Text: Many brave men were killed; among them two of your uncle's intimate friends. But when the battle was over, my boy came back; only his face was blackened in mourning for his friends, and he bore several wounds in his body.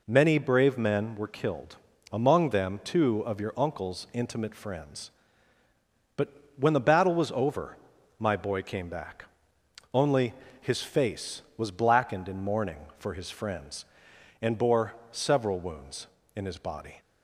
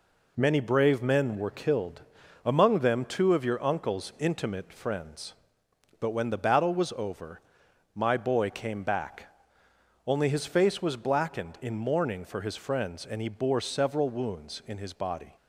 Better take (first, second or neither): second